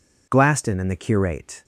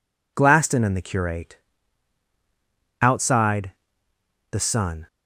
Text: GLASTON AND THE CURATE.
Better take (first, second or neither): first